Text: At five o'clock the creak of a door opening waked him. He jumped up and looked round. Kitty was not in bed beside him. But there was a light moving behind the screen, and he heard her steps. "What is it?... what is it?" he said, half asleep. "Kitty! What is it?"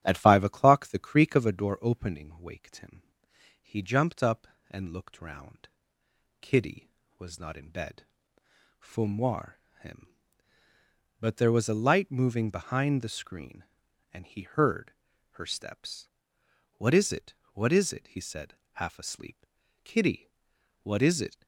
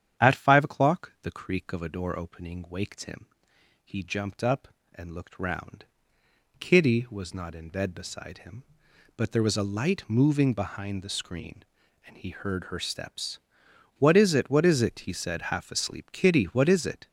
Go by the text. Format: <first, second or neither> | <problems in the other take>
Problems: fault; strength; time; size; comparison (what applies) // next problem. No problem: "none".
second | starts louder than the rest; strong; until 1.0 s; 10 dB; strong in the second // says "fumoir" for "beside"; at 8.7 s // pauses between "heard" and "her"; at 14.9 s; 0.40 s long